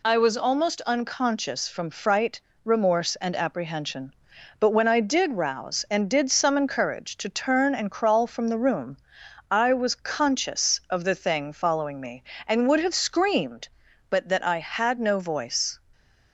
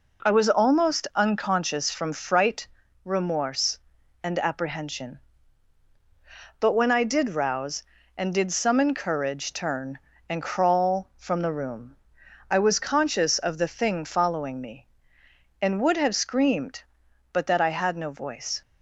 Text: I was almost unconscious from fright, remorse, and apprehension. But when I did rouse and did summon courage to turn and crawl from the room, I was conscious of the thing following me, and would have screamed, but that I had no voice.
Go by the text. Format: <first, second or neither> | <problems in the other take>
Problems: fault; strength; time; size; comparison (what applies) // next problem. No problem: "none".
first | skips "to"; at 9.5 s